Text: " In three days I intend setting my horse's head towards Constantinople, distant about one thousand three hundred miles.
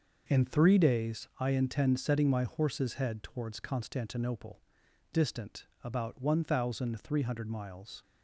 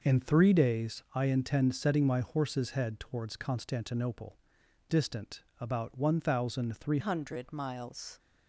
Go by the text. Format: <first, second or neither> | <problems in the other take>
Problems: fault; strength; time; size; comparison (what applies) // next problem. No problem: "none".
first | pauses between "distant" and "about"; slight; at 5.4 s; 0.16 s long; slight in the first // changes voice at "hundred"; from 7.0 s on; 1.1 s long